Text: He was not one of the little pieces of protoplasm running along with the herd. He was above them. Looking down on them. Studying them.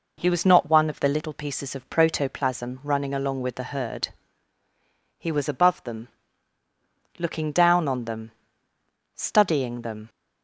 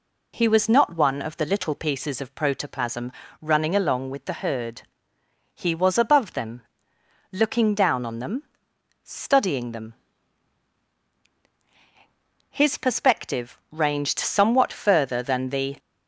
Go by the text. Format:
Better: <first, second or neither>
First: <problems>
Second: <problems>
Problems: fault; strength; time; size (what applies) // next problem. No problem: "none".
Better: first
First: none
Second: pauses between "protoplasm" and "running"; slight; at 3.1 s; 0.28 s long // goes on to say "His perspective ranged somewhat further than the"; strong; from 12.5 s on; 3.2 s long